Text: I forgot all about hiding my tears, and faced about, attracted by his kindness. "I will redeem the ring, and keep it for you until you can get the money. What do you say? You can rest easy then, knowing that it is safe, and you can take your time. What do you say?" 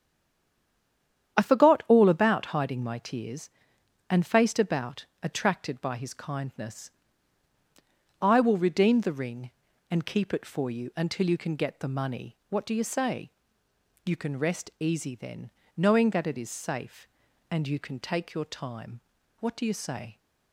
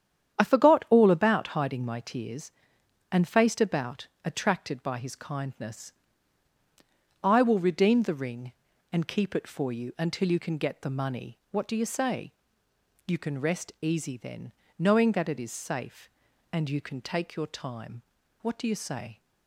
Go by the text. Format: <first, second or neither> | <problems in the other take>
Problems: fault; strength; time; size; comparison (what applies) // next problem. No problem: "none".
second | stays silent before the first word; noticeable; until 1.3 s; 1.3 s long // starts louder than the rest; strong; until 2.4 s; 9 dB; strong in the second